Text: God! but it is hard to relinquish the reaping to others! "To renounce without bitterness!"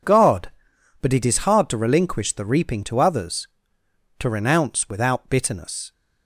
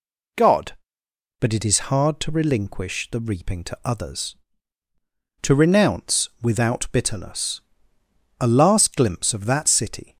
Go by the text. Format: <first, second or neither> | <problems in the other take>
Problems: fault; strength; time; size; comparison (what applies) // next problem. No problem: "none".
first | goes on to say "A last glimpse of that City"; strong; from 8.4 s on; 1.7 s long